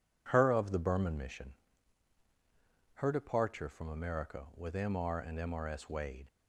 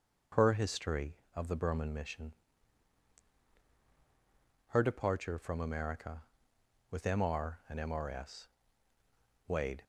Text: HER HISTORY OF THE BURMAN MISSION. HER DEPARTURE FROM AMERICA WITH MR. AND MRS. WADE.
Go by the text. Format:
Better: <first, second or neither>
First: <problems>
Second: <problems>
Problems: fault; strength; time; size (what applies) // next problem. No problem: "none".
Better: second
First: skips "HISTORY"; at 0.5 s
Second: none